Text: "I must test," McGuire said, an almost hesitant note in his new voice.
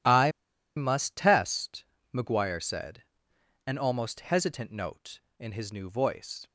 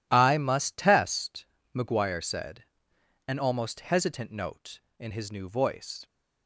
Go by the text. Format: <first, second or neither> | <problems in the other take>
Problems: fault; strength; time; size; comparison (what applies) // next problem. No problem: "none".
second | pauses between "I" and "must"; at 0.3 s; 0.45 s long